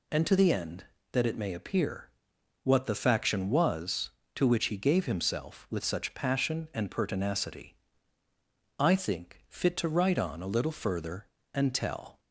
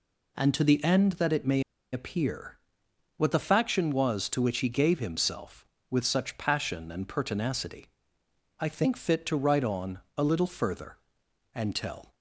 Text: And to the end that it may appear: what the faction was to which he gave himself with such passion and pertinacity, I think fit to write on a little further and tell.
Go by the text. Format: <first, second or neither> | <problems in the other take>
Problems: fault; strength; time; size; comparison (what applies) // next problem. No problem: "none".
first | pauses between "may" and "appear"; slight; at 1.6 s; 0.31 s long // pauses between "on" and "a"; slight; at 9.9 s; 0.18 s long